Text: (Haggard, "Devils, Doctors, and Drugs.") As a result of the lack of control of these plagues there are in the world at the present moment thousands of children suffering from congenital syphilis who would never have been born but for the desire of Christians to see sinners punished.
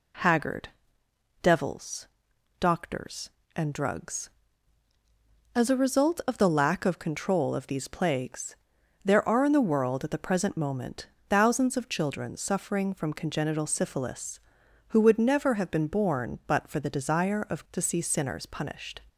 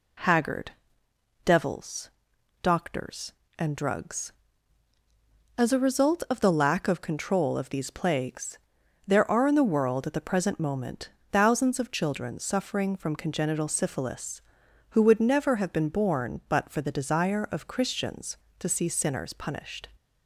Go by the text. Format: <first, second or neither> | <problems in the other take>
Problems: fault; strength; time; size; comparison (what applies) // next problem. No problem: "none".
second | pauses between "plagues" and "there"; noticeable; at 8.5 s; 0.48 s long; noticeable in the second // pauses between "moment" and "thousands"; slight; at 11.0 s; 0.20 s long; slight in the second // skips "Christians"; at 17.6 s